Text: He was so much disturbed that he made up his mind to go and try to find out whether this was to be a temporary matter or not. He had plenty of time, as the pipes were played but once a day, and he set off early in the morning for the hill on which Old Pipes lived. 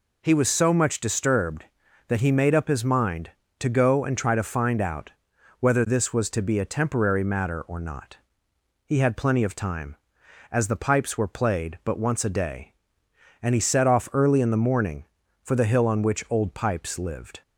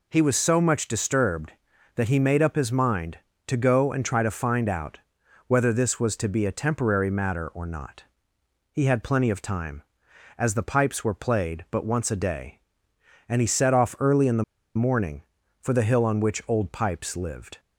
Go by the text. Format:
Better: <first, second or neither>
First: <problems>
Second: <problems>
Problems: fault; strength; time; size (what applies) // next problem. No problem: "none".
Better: first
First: pauses between "out" and "whether"; noticeable; at 5.1 s; 0.50 s long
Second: pauses between "out" and "whether"; noticeable; at 4.9 s; 0.50 s long // pauses between "the" and "morning"; slight; at 14.4 s; 0.33 s long